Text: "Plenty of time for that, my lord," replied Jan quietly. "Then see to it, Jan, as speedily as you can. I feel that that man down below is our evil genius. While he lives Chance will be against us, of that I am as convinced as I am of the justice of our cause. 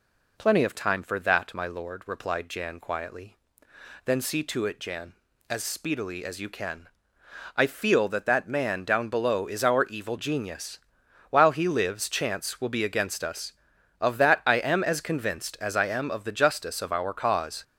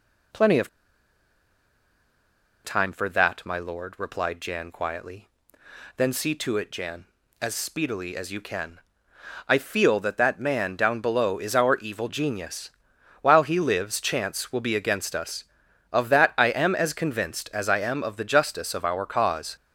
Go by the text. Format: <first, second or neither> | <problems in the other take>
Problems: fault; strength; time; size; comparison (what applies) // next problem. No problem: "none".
first | pauses between "of" and "time"; strong; at 0.6 s; 1.9 s long